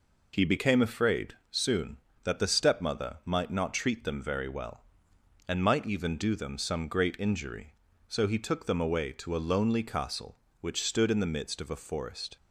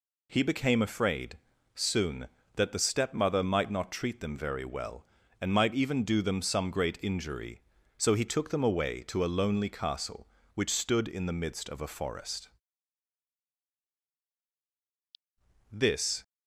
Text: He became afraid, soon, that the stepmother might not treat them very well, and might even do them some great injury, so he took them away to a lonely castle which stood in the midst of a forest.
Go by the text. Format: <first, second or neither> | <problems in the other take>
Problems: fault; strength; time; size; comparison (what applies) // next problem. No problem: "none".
first | goes on to say "This"; from 15.7 s on; 0.50 s long